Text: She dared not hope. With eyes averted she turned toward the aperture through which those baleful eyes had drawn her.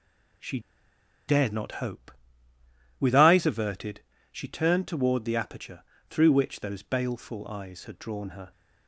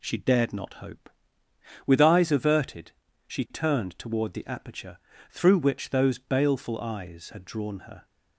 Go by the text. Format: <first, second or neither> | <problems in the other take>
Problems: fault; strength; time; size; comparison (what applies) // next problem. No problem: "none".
second | pauses between "She" and "dared"; noticeable; at 0.5 s; 0.69 s long // pauses between "averted" and "she"; slight; at 4.0 s; 0.32 s long; slight in the second // pauses between "aperture" and "through"; slight; at 5.8 s; 0.26 s long; slight in the second